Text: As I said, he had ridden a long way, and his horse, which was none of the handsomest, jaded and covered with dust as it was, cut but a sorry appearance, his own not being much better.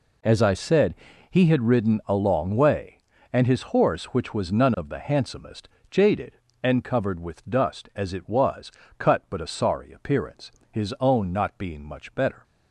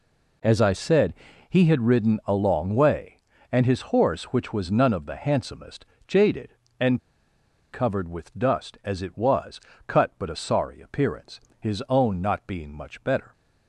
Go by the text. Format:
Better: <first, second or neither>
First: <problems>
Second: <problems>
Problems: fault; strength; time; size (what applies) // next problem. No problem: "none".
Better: first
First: none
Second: pauses between "and" and "covered"; noticeable; at 6.9 s; 0.72 s long